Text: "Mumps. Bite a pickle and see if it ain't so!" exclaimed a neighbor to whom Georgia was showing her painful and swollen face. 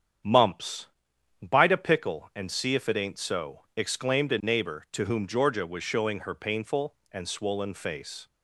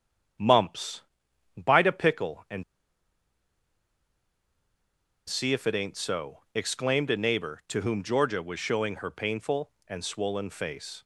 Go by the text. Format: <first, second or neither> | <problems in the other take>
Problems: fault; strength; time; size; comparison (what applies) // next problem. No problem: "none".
first | starts louder than the rest; strong; until 1.9 s; 8.5 dB; strong in the first // pauses between "and" and "see"; strong; at 2.6 s; 2.6 s long